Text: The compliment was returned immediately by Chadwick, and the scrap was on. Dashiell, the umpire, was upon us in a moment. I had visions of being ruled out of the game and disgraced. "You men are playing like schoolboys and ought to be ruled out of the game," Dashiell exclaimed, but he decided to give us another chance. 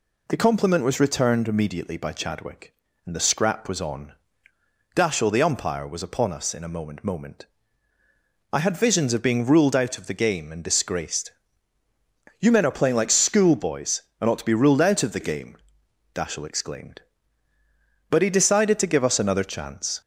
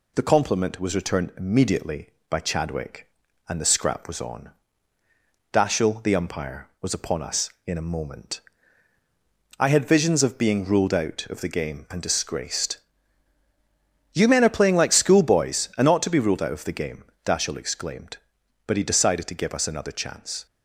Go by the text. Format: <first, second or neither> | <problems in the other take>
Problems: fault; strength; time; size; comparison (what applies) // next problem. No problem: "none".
second | says "moment" twice; at 7.0 s